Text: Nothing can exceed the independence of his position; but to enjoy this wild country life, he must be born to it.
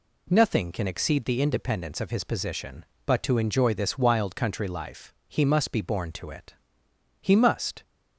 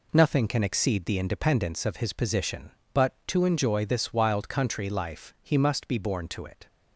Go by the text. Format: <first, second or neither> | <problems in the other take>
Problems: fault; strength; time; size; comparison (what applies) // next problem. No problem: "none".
second | goes on to say "He must"; from 7.2 s on; 0.60 s long